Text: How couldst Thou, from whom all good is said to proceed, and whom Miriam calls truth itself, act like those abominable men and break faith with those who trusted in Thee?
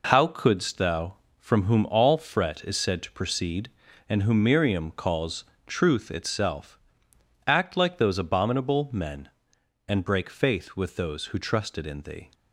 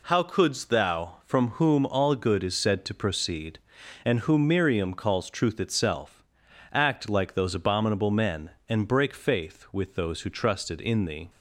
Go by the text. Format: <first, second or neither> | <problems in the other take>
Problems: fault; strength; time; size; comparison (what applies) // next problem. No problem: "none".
second | says "fret" for "good"; at 2.1 s // pauses between "calls" and "truth"; slight; at 5.4 s; 0.20 s long